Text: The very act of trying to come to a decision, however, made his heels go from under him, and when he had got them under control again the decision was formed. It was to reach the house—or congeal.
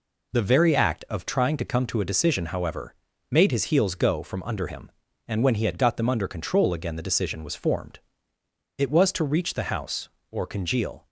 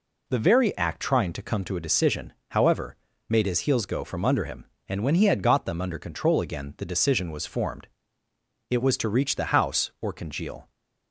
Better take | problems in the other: first | skips "of"; at 1.0 s

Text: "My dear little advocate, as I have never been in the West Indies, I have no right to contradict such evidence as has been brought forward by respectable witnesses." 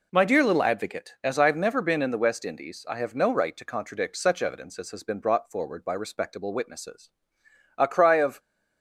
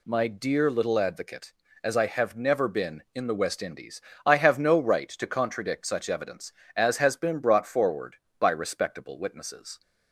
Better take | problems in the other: second | goes on to say "A cry of"; noticeable; from 7.7 s on; 0.64 s long

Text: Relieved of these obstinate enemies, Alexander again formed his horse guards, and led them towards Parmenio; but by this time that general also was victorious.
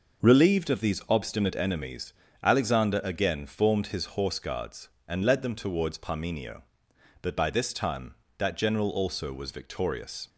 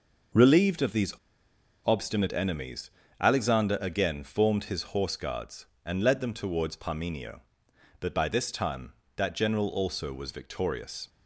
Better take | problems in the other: first | pauses between "these" and "obstinate"; noticeable; at 1.1 s; 0.73 s long

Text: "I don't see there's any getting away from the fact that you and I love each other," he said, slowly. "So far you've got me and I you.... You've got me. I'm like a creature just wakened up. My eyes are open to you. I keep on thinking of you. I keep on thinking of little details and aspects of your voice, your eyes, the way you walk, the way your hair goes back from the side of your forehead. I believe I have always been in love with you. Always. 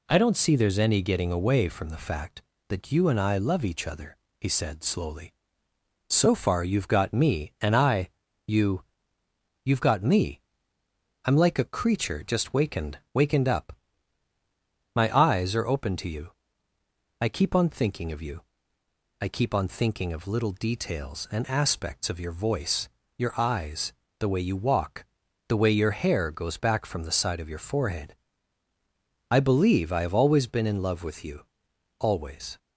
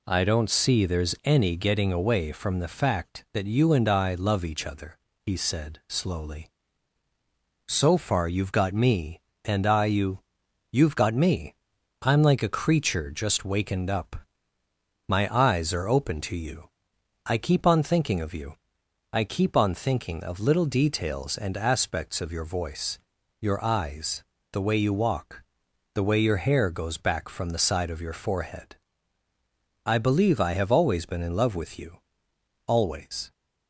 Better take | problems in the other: second | pauses between "I" and "you"; at 8.0 s; 0.38 s long // says "wakened" twice; at 13.1 s

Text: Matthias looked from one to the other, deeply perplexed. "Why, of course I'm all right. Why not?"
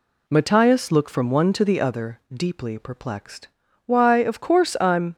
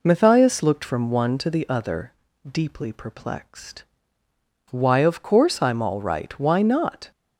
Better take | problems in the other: second | stops before "all right Why not"; at 5.1 s

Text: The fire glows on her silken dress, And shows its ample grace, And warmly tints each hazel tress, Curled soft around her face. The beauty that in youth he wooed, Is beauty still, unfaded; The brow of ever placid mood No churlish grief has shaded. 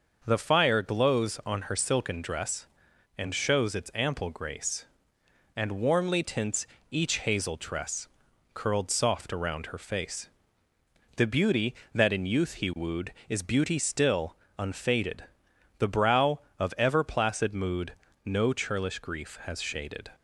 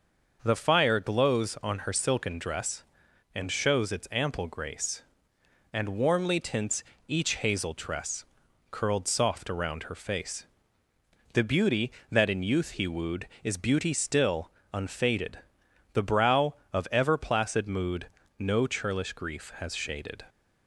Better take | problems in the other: neither | starts louder than the rest; the same in both // pauses between "tints" and "each"; slight; the same in both // pauses between "mood" and "No"; slight; the same in both

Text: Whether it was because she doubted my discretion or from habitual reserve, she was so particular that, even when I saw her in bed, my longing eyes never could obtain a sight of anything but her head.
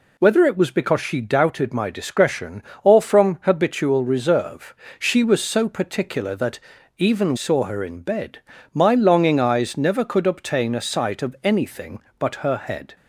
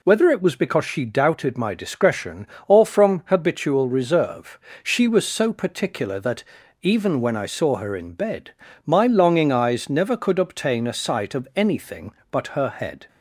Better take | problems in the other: second | skips "when I"; at 7.3 s

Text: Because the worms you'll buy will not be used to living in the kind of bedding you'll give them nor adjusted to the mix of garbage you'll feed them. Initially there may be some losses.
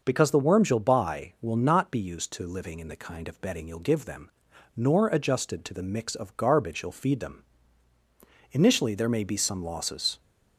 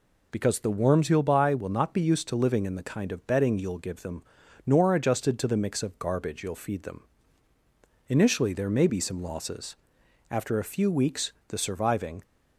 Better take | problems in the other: first | pauses between "them" and "nor"; at 4.2 s; 0.44 s long; also in the first // goes on to say "After a few weeks the surviving"; strong; from 10.2 s on; 1.9 s long

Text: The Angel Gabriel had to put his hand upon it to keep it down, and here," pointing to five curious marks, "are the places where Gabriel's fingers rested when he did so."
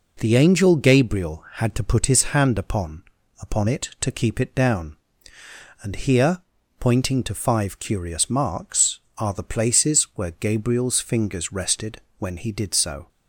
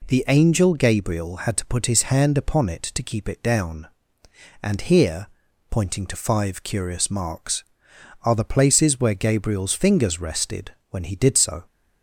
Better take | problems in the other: second | says "upon" twice; at 3.4 s // pauses between "rested" and "when"; slight; at 12.0 s; 0.18 s long; slight in the second

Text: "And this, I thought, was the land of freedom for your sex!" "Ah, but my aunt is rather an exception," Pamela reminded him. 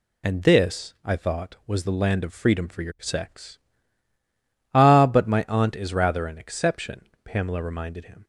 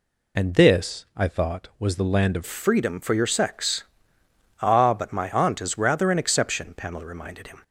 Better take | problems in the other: first | changes voice at "freedom"; from 2.4 s on; 5.2 s long

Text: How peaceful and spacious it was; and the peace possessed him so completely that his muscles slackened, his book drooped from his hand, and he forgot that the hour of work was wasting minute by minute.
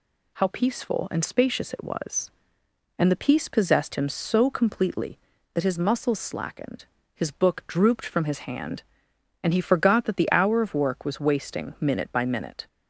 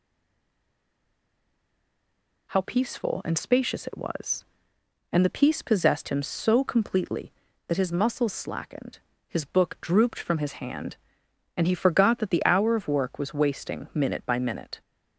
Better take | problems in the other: first | stays silent before the first word; until 2.4 s; 2.4 s long

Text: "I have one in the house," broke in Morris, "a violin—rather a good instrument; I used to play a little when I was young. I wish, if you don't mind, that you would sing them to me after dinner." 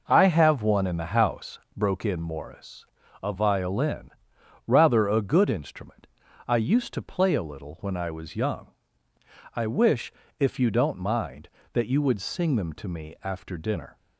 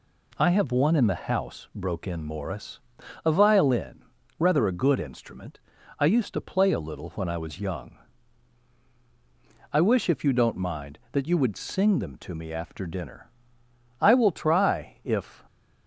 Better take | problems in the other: first | goes on to say "I will try if"; from 14.0 s on; 1.4 s long

